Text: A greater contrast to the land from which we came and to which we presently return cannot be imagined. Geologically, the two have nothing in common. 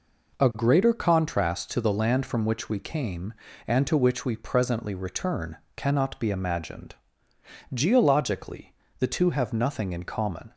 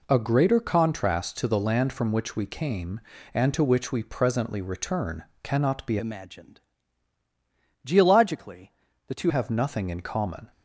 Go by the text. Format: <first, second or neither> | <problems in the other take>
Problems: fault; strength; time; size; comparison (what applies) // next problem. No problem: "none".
first | pauses between "return" and "cannot"; slight; at 5.2 s; 0.20 s long; slight in the first // changes voice from "imagined" to "two"; from 5.9 to 9.2 s; 3.3 s long